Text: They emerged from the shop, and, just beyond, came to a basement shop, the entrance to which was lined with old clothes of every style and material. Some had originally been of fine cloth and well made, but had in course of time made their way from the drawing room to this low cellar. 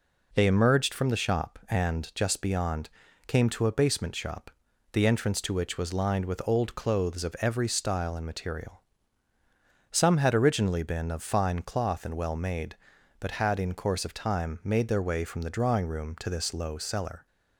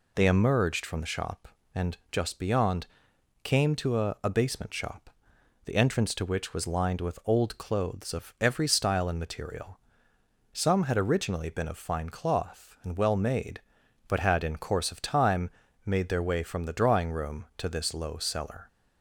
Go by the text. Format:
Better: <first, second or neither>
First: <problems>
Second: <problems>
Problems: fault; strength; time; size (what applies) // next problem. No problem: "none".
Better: first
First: none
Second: says "a" twice; at 4.2 s // pauses between "time" and "made"; slight; at 15.4 s; 0.36 s long